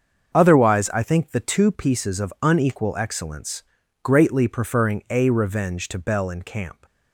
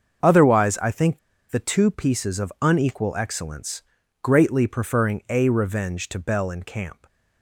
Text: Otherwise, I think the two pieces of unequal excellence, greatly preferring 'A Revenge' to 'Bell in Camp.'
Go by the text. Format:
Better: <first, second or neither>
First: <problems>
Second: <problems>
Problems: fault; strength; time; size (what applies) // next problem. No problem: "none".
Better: first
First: starts louder than the rest; until 1.3 s; 6.5 dB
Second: starts louder than the rest; until 1.5 s; 6.5 dB // pauses between "think" and "the"; slight; at 1.1 s; 0.32 s long